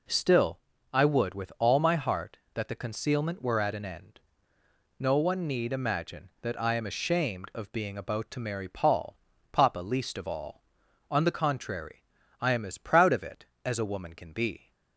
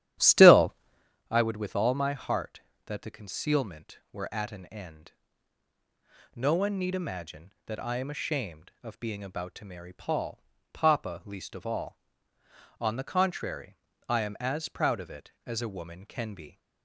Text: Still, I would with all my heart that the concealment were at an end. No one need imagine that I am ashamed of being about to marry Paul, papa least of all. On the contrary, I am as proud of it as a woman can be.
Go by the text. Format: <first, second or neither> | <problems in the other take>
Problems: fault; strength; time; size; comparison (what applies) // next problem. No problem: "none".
first | starts louder than the rest; strong; until 1.2 s; 11.5 dB